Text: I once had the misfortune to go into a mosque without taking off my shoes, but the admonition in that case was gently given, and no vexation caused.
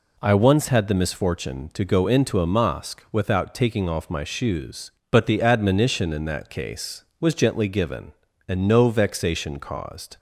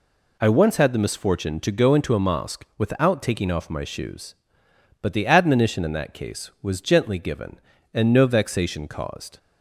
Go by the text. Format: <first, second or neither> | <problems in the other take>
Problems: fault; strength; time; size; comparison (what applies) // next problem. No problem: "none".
neither | none